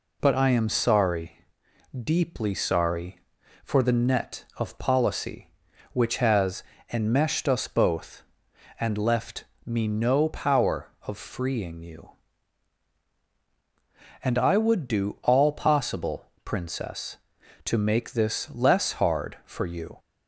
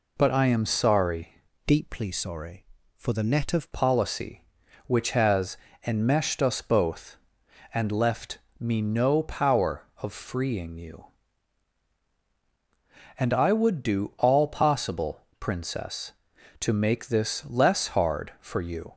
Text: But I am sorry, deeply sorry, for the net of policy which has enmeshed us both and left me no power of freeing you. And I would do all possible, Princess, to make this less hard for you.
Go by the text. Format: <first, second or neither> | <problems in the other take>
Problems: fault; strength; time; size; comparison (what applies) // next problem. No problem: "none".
first | changes voice from "deeply" to "of"; from 1.6 to 3.7 s; 2.1 s long // pauses between "has" and "enmeshed"; slight; at 5.5 s; 0.30 s long; slight in the first // pauses between "left" and "me"; slight; at 8.3 s; 0.20 s long; slight in the first